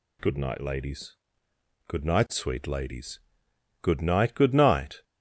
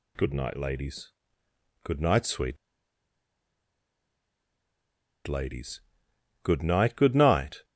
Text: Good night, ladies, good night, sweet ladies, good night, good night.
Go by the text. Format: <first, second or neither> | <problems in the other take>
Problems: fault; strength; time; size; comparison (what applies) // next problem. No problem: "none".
first | pauses between "sweet" and "ladies"; strong; at 2.5 s; 2.6 s long